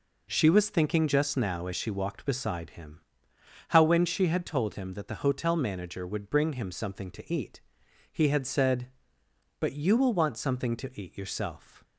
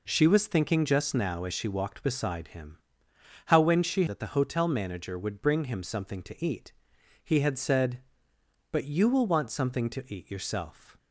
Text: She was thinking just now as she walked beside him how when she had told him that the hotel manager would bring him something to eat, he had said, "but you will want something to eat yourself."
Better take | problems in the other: first | pauses between "him" and "how"; noticeable; at 2.7 s; 0.68 s long; noticeable in the first // skips "had told him"; at 4.0 s

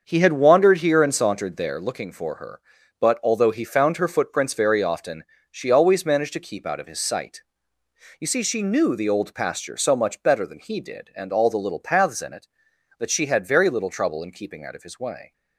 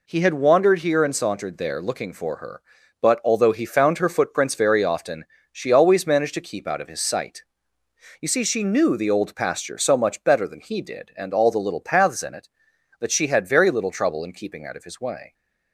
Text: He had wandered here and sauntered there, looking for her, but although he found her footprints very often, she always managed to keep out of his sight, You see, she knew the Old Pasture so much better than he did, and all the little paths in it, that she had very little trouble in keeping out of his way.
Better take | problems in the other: second | starts louder than the rest; until 1.7 s; 6.5 dB

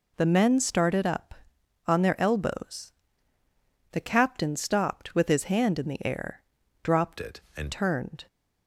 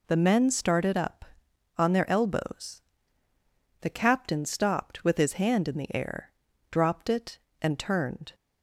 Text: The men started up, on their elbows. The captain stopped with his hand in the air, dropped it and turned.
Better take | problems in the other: second | changes voice from "it" to "and"; from 7.1 to 7.7 s; 0.6 s long

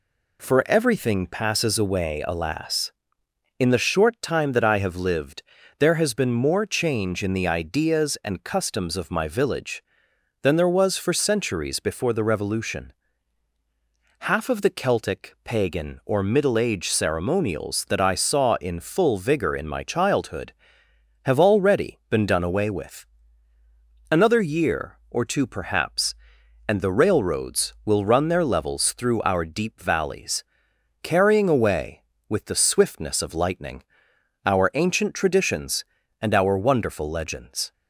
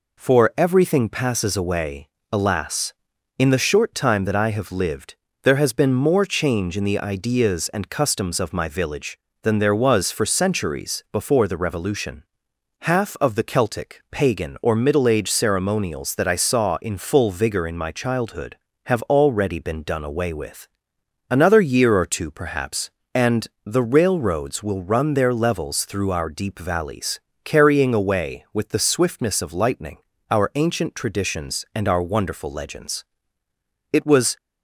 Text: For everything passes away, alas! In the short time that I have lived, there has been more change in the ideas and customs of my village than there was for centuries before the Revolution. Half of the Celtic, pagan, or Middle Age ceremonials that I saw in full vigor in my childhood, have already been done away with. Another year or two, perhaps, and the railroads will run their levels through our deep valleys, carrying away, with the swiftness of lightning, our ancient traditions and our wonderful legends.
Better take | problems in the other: first | pauses between "and" and "the"; slight; at 23.4 s; 0.20 s long // goes on to say "It was"; slight; from 33.9 s on; 0.44 s long

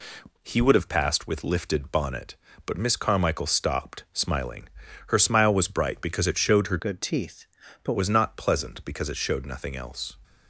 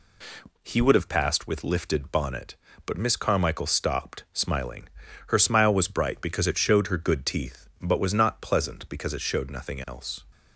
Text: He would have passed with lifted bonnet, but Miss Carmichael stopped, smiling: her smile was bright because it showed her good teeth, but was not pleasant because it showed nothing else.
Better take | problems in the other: second | changes voice from "good" to "but"; from 6.7 to 7.9 s; 1.2 s long

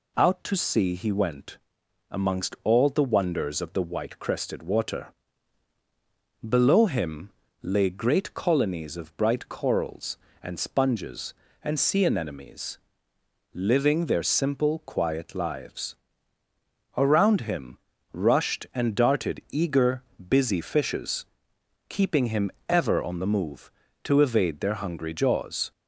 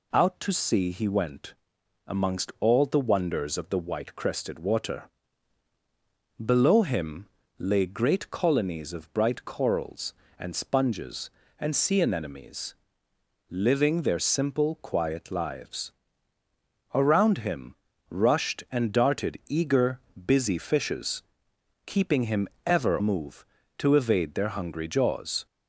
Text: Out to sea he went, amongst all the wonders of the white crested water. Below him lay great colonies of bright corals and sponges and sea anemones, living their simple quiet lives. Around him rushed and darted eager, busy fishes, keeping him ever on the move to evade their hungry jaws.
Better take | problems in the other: first | pauses between "him" and "lay"; slight; at 7.2 s; 0.32 s long; slight in the first // pauses between "him" and "rushed"; slight; at 17.7 s; 0.34 s long; slight in the first // pauses between "him" and "ever"; slight; at 22.4 s; 0.18 s long; slight in the first // skips "on the"; at 22.9 s

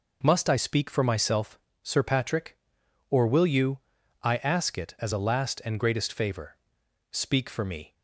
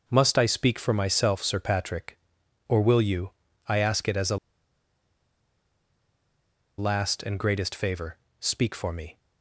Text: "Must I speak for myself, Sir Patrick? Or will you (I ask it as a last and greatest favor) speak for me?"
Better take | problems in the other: first | pauses between "a" and "last"; strong; at 4.3 s; 2.4 s long

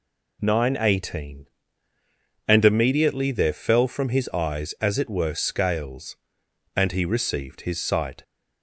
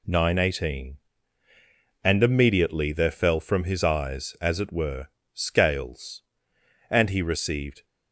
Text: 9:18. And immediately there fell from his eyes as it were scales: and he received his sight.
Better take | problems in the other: first | pauses between "were" and "scales"; noticeable; at 5.0 s; 0.50 s long // stops before "his sight"; at 7.8 s

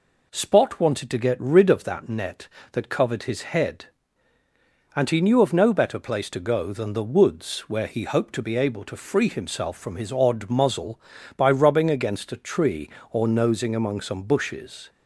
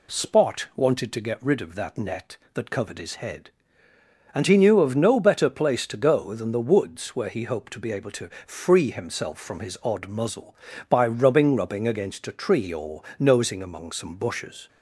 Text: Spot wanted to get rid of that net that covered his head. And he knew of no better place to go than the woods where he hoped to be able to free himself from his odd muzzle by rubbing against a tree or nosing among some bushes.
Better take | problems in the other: first | pauses between "to" and "free"; slight; at 8.2 s; 0.16 s long // says "rubbing" twice; at 11.5 s // pauses between "or" and "nosing"; slight; at 13.0 s; 0.16 s long

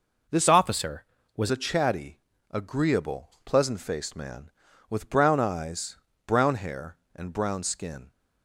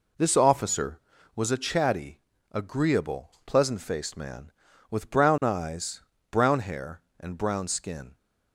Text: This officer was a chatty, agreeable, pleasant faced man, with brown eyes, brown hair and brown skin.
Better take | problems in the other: second | changes voice from "officer" to "was"; from 0.4 to 1.5 s; 1.1 s long

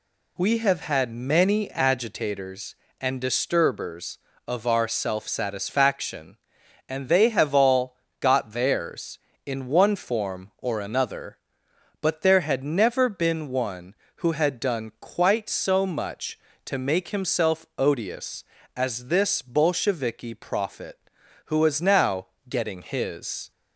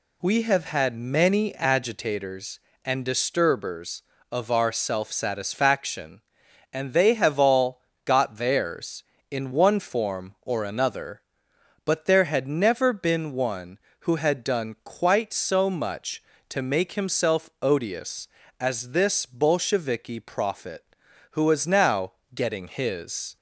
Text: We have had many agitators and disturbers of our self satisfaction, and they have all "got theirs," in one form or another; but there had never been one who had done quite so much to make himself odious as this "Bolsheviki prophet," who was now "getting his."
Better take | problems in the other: neither | pauses between "all" and "got"; slight; the same in both // pauses between "now" and "getting"; slight; the same in both

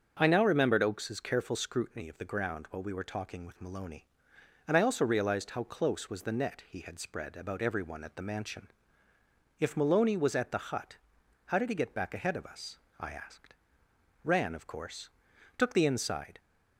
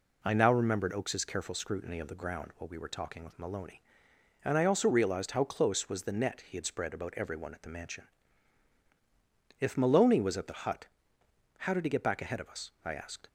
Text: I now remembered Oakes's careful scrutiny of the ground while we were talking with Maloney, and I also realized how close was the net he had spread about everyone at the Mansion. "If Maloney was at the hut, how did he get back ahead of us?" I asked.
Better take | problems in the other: second | starts louder than the rest; strong; until 1.2 s; 7 dB // goes on to say "Ran of course took the inside"; strong; from 14.2 s on; 2.1 s long

